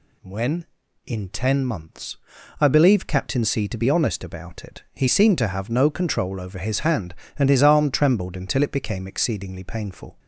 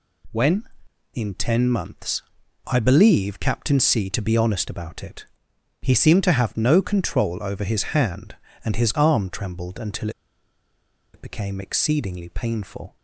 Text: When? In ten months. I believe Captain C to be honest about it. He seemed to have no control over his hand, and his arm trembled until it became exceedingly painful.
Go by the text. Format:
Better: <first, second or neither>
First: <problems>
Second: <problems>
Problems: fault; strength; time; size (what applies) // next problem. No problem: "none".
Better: first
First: none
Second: pauses between "until" and "it"; at 10.0 s; 1.0 s long